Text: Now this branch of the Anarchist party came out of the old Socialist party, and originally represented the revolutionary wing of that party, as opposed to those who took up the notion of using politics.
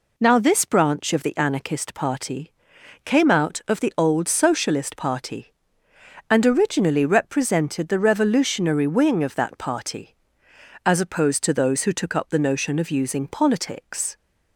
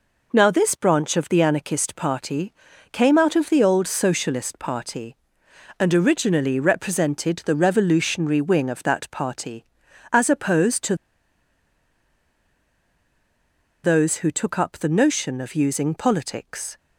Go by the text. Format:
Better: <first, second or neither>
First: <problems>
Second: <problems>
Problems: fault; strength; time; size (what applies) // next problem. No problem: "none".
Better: first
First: pauses between "party" and "came"; noticeable; at 2.5 s; 0.50 s long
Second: pauses between "party" and "came"; at 2.5 s; 0.40 s long // pauses between "to" and "those"; strong; at 10.9 s; 2.8 s long